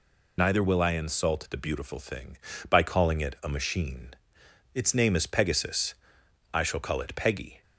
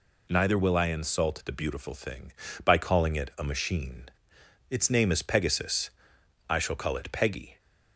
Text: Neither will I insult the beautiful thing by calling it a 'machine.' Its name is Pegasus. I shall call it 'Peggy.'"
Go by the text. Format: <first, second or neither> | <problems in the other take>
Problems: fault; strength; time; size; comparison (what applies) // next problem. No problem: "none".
second | loses the start of "Neither"; at 0.3 s; 40 ms